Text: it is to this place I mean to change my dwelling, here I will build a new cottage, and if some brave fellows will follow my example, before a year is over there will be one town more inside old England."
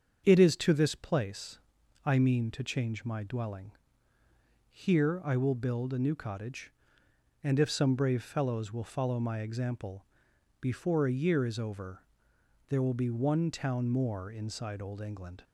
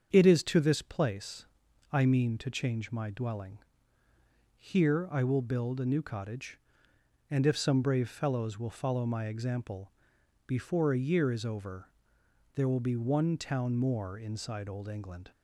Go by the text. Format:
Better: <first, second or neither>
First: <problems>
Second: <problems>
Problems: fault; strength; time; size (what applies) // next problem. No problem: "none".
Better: neither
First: starts louder than the rest; strong; until 1.2 s; 7.5 dB // pauses between "place" and "I"; at 1.5 s; 0.44 s long // pauses between "over" and "there"; noticeable; at 12.0 s; 0.68 s long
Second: starts louder than the rest; strong; until 1.1 s; 7 dB // pauses between "place" and "I"; at 1.4 s; 0.44 s long // pauses between "over" and "there"; noticeable; at 11.8 s; 0.68 s long